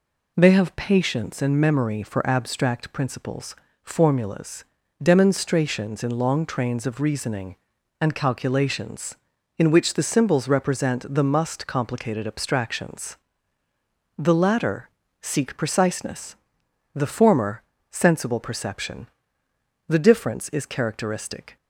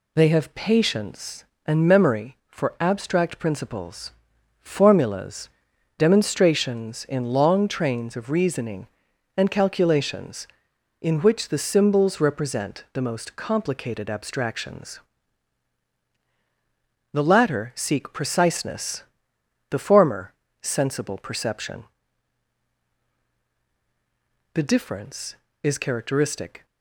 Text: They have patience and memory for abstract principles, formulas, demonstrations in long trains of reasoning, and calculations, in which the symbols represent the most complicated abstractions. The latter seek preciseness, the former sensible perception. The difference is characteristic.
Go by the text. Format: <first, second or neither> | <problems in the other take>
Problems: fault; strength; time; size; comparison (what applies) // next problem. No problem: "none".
second | says "must" for "most"; at 11.2 s // pauses between "latter" and "seek"; slight; at 14.8 s; 0.32 s long // pauses between "former" and "sensible"; slight; at 17.6 s; 0.30 s long; slight in the second